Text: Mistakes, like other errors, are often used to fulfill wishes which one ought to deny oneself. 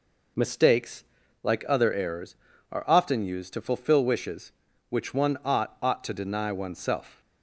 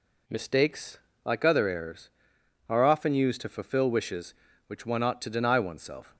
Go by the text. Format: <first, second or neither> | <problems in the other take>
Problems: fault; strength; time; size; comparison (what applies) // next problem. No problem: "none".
second | says "ought" twice; at 5.8 s